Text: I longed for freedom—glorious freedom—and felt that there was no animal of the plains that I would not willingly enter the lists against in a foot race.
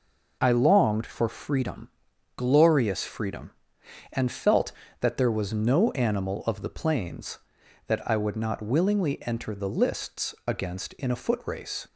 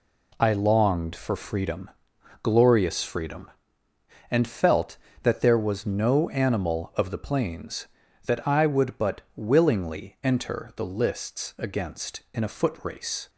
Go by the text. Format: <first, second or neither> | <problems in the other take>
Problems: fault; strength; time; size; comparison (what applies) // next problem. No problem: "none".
first | says "but" for "not"; at 8.9 s